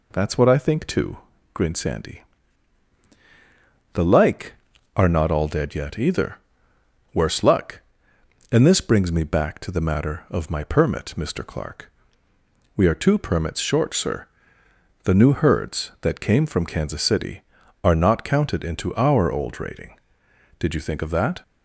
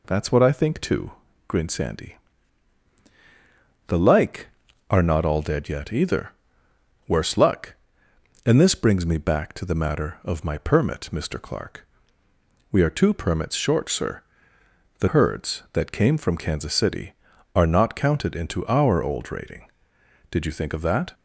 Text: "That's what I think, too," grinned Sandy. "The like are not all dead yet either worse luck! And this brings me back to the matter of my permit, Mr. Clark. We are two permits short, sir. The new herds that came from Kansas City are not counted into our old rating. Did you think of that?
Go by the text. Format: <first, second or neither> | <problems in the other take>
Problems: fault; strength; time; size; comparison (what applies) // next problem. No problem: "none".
first | pauses between "either" and "worse"; noticeable; at 6.3 s; 0.76 s long; noticeable in the first // skips "new"; at 15.0 s